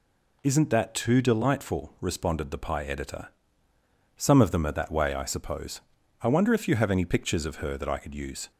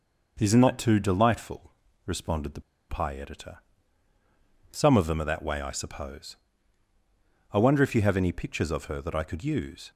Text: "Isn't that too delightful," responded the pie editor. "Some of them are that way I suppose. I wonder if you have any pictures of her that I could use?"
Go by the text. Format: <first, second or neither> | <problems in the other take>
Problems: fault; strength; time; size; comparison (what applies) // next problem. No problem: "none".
first | pauses between "the" and "pie"; slight; at 2.5 s; 0.29 s long